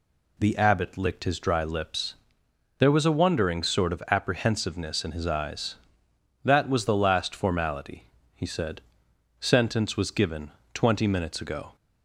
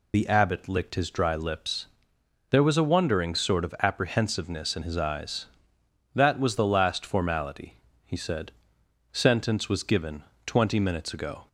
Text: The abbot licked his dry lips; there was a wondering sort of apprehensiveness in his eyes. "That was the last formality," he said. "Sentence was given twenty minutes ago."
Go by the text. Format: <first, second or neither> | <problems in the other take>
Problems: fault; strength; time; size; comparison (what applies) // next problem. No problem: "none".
first | loses the start of "The"; at 0.1 s; 40 ms // pauses between "given" and "twenty"; slight; at 10.2 s; 0.22 s long; slight in the first